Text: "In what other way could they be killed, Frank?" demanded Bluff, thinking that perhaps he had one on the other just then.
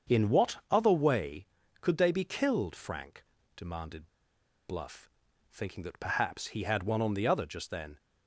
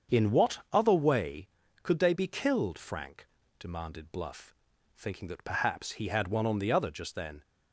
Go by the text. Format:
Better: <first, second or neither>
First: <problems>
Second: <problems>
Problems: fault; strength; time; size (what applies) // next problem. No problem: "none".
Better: second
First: starts louder than the rest; until 1.2 s; 7 dB // pauses between "demanded" and "Bluff"; noticeable; at 4.0 s; 0.59 s long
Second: starts louder than the rest; until 1.2 s; 7 dB